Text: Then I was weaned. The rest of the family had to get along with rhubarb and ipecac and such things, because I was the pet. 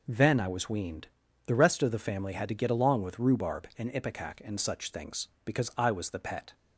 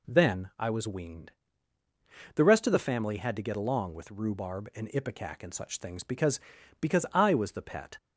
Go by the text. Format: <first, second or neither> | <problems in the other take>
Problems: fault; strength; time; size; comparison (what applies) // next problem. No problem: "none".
first | says "because" twice; at 6.8 s